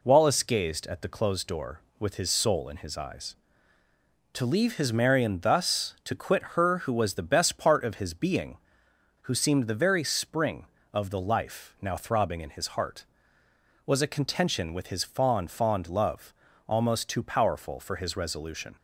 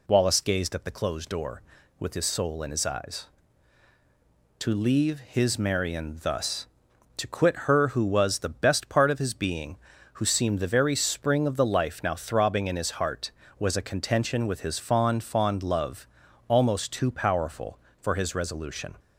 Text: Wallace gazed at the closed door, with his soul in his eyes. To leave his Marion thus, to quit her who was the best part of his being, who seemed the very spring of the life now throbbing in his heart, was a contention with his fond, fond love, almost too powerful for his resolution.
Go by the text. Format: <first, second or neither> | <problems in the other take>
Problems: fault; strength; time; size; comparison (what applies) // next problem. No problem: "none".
neither | none